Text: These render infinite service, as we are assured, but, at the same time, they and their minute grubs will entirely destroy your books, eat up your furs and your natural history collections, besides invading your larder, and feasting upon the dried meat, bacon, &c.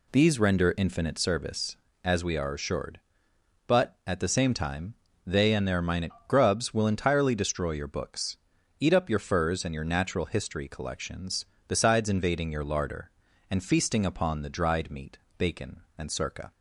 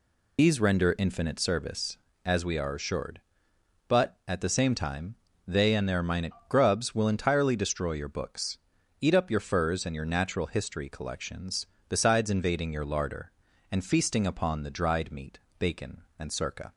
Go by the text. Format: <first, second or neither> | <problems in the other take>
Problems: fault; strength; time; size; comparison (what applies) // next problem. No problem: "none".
first | loses the start of "These"; at 0.3 s; 80 ms // pauses between "minute" and "grubs"; slight; at 6.3 s; 0.16 s long; slight in the first